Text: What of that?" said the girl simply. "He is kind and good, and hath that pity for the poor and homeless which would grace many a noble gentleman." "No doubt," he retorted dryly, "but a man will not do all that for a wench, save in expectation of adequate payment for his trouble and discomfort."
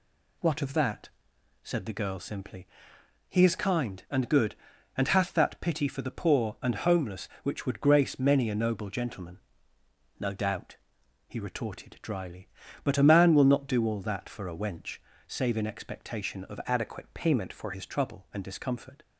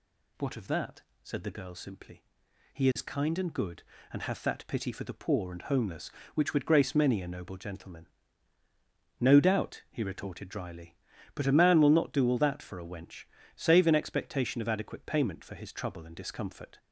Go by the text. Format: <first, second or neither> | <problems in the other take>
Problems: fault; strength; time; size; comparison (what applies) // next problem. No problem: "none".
second | changes voice from "adequate" to "for"; from 16.6 to 17.7 s; 1.1 s long